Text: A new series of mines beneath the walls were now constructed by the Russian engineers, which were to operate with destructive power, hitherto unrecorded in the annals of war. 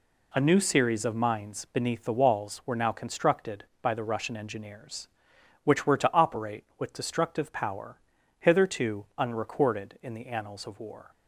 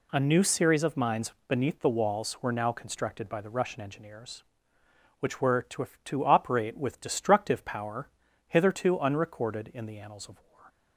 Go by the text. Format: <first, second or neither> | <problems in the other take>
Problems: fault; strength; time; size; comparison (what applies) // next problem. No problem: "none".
first | says "to" twice; at 6.0 s